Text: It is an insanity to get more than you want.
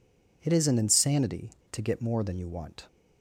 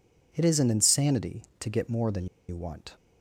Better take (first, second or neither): first